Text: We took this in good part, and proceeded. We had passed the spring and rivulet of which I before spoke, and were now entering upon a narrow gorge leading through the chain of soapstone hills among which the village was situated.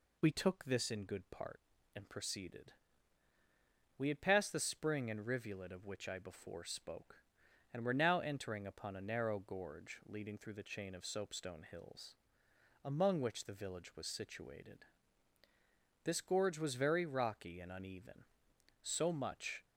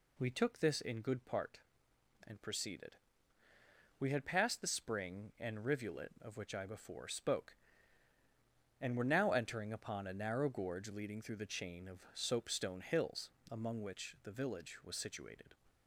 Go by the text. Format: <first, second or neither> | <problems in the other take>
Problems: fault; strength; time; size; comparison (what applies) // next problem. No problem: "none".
second | pauses between "hills" and "among"; noticeable; at 12.1 s; 0.70 s long; slight in the second // goes on to say "This gorge was very rocky and uneven so much"; strong; from 16.0 s on; 3.6 s long